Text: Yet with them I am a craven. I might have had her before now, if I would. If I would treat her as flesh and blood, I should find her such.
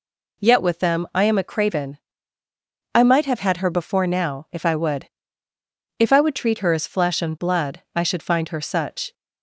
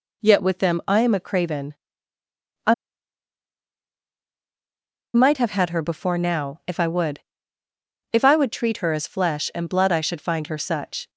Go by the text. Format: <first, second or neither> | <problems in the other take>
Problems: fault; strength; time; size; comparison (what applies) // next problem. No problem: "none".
first | pauses between "I" and "might"; strong; at 2.7 s; 2.4 s long